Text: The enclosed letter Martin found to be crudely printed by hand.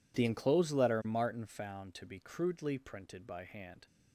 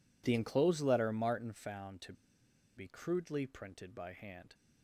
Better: first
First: none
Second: pauses between "to" and "be"; noticeable; at 2.1 s; 0.64 s long

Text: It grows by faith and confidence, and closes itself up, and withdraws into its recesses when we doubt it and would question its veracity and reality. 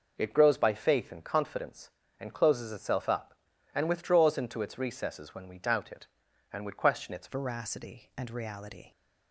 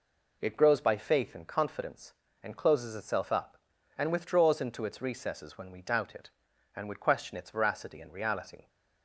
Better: second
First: changes voice at "veracity"; from 7.2 s on; 1.7 s long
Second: none

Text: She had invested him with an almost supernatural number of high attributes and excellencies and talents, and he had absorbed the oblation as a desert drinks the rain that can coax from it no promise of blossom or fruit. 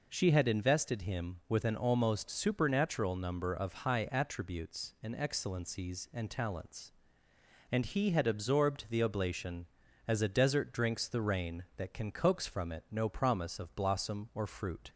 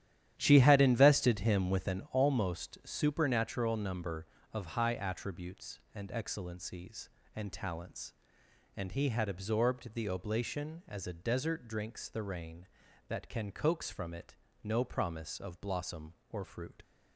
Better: first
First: none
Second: starts louder than the rest; strong; until 2.1 s; 11 dB // pauses between "it" and "no"; slight; at 14.3 s; 0.26 s long

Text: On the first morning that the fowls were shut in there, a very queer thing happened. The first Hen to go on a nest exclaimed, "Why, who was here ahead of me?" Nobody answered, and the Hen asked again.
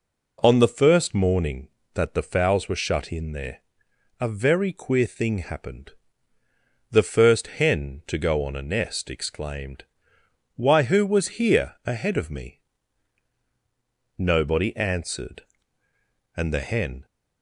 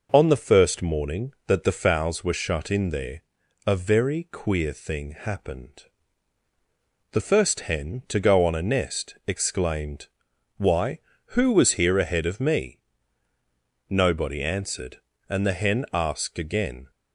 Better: second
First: stops before "asked again"; at 17.0 s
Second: none

